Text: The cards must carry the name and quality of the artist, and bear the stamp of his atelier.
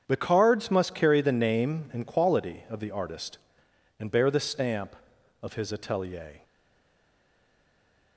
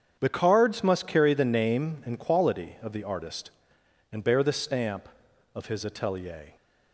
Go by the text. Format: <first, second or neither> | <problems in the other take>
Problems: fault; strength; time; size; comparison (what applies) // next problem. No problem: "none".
second | starts louder than the rest; strong; until 1.0 s; 8 dB; strong in the second // stays silent after the last word; noticeable; from 6.4 s on; 1.7 s long